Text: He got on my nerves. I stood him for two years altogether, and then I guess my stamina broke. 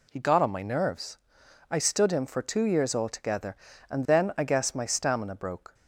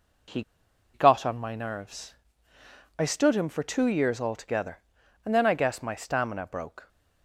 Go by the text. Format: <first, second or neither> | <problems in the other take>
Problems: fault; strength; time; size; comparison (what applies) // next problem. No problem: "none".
first | pauses between "He" and "got"; noticeable; at 0.4 s; 0.50 s long